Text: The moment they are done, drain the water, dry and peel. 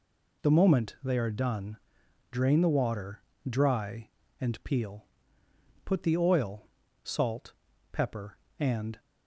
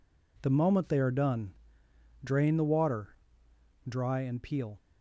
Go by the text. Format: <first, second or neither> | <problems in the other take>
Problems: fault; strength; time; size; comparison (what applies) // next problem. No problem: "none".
second | goes on to say "Put the oil salt pepper and"; strong; from 5.8 s on; 3.1 s long